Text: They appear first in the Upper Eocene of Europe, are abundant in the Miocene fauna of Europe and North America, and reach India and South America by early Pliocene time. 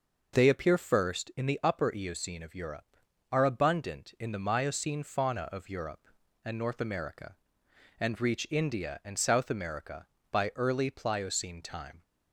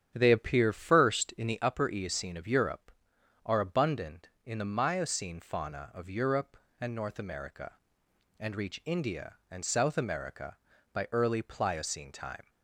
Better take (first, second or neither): first